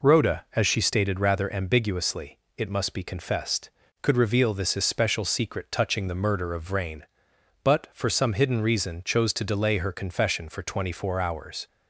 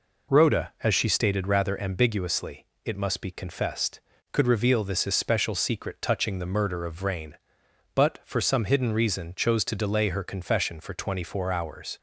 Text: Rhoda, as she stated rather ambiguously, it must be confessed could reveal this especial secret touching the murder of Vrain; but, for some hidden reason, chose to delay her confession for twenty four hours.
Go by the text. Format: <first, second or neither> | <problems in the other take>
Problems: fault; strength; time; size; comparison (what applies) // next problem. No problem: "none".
neither | none